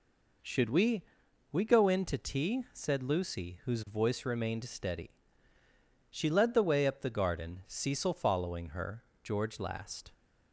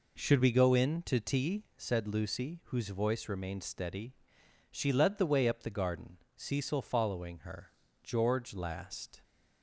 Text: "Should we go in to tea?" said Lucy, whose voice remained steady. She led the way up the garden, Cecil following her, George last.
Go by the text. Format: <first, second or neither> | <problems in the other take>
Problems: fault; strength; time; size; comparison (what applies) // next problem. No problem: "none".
second | says "we" twice; at 1.5 s